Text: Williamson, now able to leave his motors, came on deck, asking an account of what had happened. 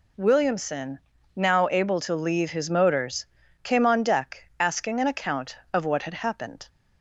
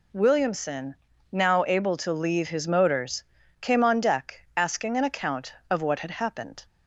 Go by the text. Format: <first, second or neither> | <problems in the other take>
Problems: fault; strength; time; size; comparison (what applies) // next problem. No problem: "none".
neither | none